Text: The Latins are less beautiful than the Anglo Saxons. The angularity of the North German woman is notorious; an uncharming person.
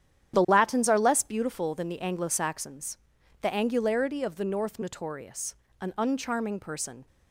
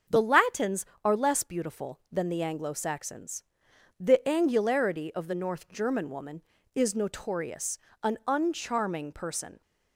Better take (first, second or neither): second